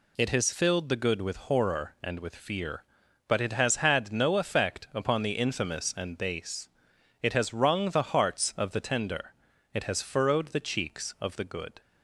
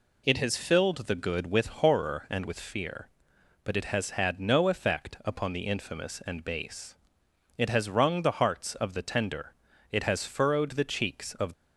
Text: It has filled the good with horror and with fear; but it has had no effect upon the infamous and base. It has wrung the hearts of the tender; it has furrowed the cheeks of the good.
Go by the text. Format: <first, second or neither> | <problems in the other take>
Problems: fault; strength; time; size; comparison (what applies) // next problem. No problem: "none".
first | stops before "the good"; at 11.5 s